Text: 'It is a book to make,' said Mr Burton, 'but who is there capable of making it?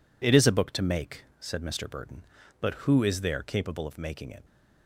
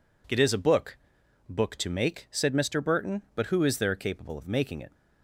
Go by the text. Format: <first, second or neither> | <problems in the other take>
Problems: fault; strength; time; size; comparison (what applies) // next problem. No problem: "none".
first | says "book" twice; at 1.4 s